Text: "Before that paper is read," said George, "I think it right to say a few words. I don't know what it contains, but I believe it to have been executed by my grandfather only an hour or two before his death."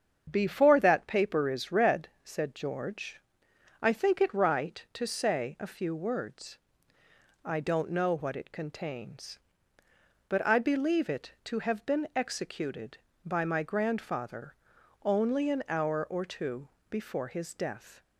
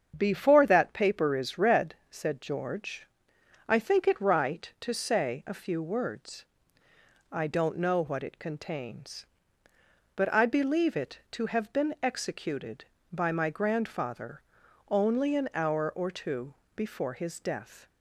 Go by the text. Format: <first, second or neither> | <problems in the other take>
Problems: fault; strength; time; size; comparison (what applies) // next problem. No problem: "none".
neither | starts louder than the rest; strong; the same in both // pauses between "grandfather" and "only"; noticeable; the same in both // pauses between "two" and "before"; slight; the same in both